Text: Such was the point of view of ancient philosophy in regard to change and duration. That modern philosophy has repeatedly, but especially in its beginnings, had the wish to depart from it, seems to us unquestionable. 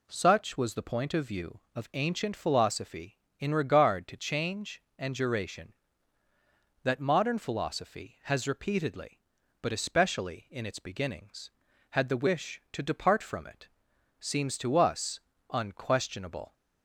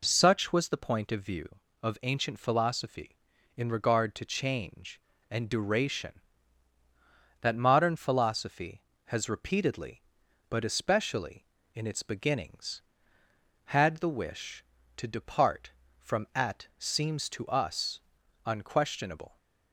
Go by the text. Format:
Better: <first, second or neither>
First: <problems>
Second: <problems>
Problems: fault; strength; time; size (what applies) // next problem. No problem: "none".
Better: first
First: pauses between "us" and "unquestionable"; slight; at 15.2 s; 0.30 s long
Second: says "at" for "it"; at 16.3 s // pauses between "us" and "unquestionable"; at 18.0 s; 0.42 s long